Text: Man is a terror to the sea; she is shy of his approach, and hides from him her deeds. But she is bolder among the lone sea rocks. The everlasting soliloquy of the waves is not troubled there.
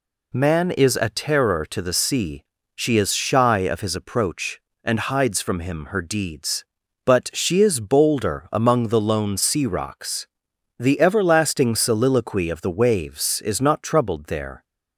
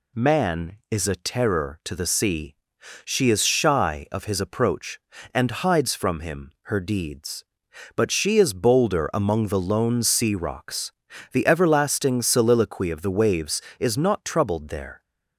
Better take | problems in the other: neither | none

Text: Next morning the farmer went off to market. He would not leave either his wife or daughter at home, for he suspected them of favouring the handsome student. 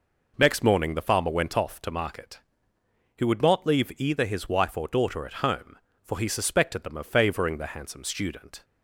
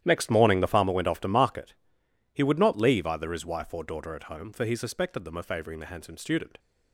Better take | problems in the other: first | gets quieter; strong; throughout; 15 dB

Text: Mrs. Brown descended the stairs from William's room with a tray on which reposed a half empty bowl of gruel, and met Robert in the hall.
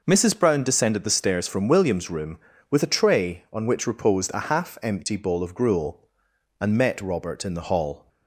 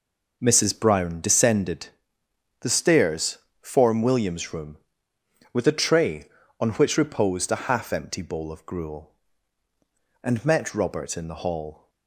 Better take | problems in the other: first | pauses between "descended" and "the"; noticeable; at 1.8 s; 0.72 s long // says "form" for "from"; at 3.6 s

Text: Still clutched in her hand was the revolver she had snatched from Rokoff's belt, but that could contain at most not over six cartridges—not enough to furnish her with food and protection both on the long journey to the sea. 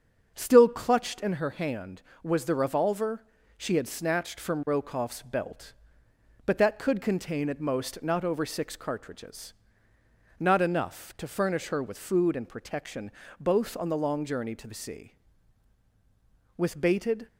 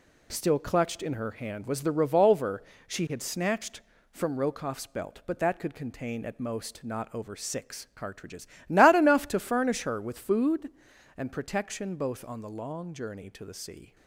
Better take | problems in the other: second | starts louder than the rest; strong; until 1.3 s; 7 dB // pauses between "revolver" and "she"; slight; at 3.2 s; 0.34 s long; slight in the second // pauses between "protection" and "both"; slight; at 13.1 s; 0.28 s long // goes on to say "With bated"; noticeable; from 16.5 s on; 0.70 s long

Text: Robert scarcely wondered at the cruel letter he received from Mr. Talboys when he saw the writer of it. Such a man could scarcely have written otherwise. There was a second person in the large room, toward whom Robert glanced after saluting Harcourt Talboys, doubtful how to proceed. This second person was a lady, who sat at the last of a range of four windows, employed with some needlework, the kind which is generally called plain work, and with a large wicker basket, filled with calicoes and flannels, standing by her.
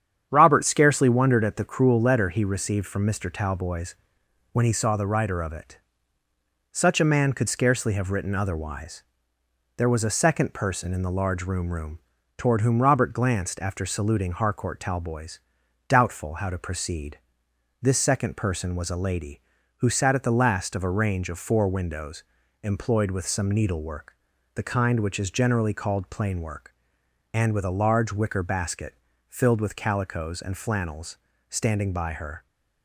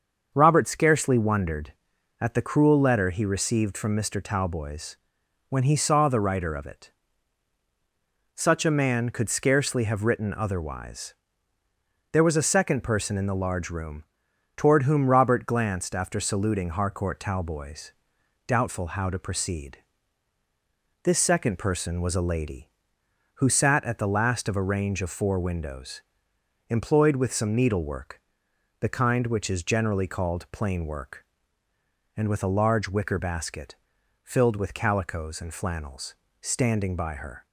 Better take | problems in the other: second | starts louder than the rest; strong; until 1.3 s; 8.5 dB; also in the second // pauses between "Talboys" and "when"; noticeable; at 3.9 s; 0.58 s long; noticeable in the second // says "room" twice; at 11.7 s

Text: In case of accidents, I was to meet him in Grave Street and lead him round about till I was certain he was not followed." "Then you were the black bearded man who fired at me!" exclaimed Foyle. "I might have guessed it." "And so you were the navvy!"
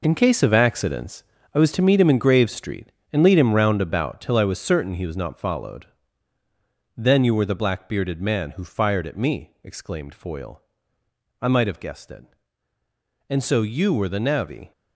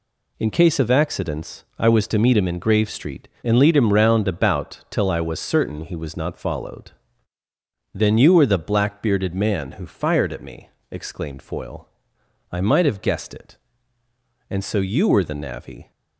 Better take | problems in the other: second | gets quieter; strong; throughout; 9.5 dB

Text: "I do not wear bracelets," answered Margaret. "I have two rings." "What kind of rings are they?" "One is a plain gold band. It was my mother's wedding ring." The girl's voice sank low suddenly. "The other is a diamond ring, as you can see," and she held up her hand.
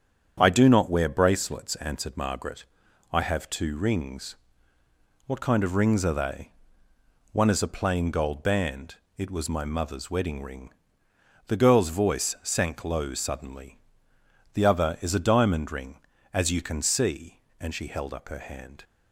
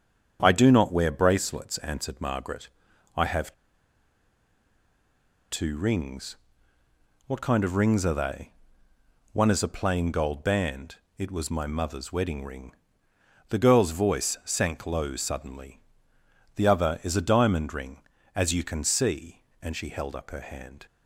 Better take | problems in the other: first | starts louder than the rest; strong; until 1.4 s; 8.5 dB; strong in the first // pauses between "have" and "two"; strong; at 3.5 s; 1.9 s long

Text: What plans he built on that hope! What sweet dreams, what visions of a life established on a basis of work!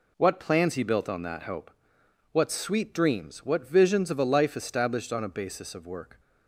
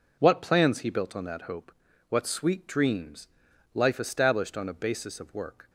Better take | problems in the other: first | skips "what visions of a"; at 3.5 s

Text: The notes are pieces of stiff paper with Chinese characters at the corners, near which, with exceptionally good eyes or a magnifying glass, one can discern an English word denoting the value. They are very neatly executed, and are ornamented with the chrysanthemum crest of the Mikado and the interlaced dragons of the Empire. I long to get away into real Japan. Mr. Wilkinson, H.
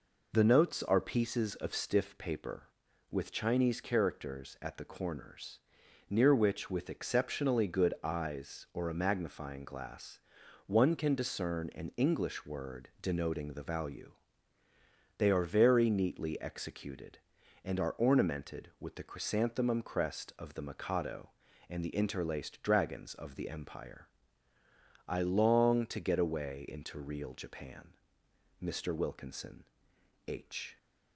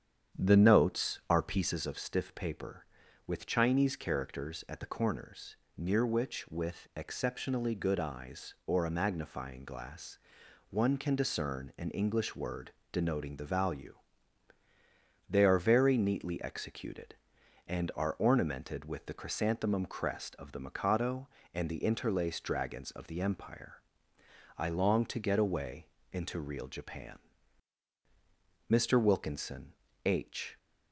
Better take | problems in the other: first | starts louder than the rest; strong; until 1.8 s; 8.5 dB // pauses between "word" and "denoting"; slight; at 12.7 s; 0.20 s long // pauses between "away" and "into"; slight; at 25.8 s; 0.26 s long

